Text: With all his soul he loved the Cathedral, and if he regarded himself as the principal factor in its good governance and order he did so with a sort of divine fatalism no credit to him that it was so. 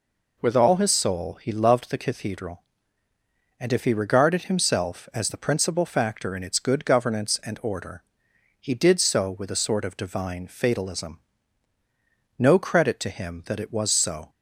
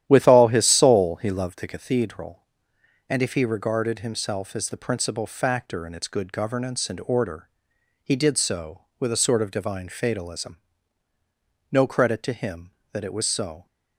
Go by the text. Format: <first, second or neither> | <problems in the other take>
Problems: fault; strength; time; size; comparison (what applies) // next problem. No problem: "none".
first | starts louder than the rest; strong; until 2.0 s; 11 dB // pauses between "order" and "he"; noticeable; at 7.4 s; 0.56 s long; noticeable in the first // pauses between "fatalism" and "no"; at 10.5 s; 1.1 s long; also in the first